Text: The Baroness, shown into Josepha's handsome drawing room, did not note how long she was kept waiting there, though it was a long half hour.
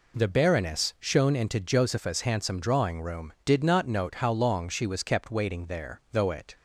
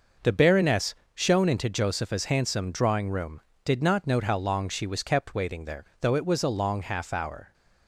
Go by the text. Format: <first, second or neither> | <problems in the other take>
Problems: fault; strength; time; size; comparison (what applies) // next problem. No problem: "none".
second | stops before "was a long half hour"; at 6.5 s